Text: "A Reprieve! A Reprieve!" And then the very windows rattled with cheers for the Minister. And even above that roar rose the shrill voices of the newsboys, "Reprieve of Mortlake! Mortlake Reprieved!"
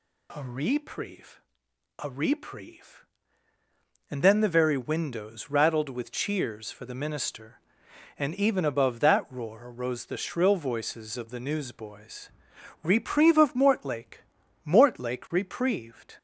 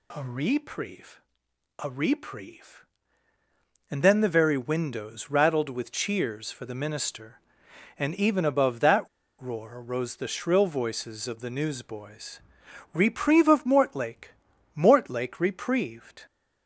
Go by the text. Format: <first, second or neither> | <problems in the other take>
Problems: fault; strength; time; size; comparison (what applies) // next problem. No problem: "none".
first | pauses between "that" and "roar"; slight; at 9.0 s; 0.31 s long